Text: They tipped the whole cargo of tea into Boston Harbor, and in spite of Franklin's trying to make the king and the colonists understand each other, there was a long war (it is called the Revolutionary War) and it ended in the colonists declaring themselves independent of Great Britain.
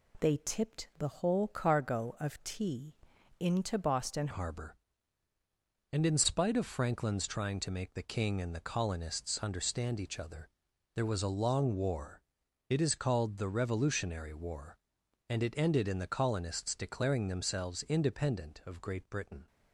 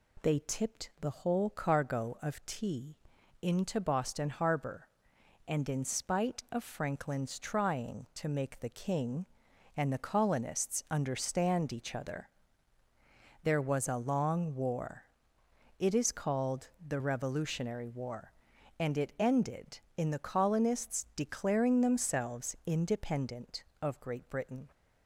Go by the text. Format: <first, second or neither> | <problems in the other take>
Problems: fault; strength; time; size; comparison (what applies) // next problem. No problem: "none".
second | pauses between "tea" and "into"; at 2.9 s; 0.44 s long; also in the second // changes voice at "Harbor"; from 4.3 s on; 15.1 s long